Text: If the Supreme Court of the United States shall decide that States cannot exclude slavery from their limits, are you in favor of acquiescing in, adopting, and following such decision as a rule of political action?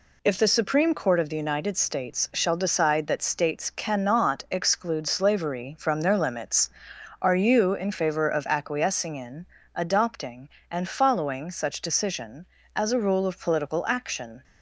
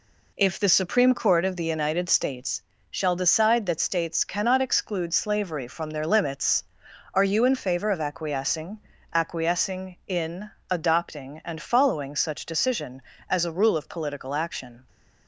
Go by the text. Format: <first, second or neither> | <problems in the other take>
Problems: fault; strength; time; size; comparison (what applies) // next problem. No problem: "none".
first | pauses between "States" and "shall"; slight; at 2.6 s; 0.26 s long // says "acquiescing" twice; at 9.1 s